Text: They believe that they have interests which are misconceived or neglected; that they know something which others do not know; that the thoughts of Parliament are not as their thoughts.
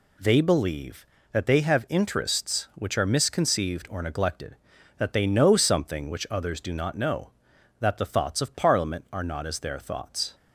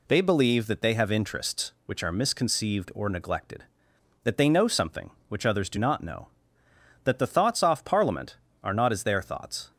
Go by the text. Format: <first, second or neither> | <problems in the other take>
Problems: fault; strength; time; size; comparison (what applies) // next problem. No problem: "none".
first | says "off" for "of"; at 7.6 s